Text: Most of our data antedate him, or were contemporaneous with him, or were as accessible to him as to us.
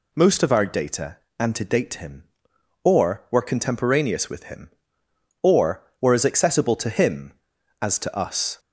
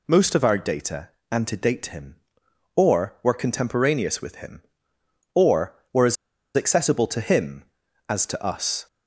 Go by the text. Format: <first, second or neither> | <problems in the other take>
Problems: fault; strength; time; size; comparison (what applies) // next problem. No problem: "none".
first | pauses between "data" and "antedate"; slight; at 1.0 s; 0.22 s long; slight in the first // pauses between "as" and "accessible"; at 6.1 s; 0.41 s long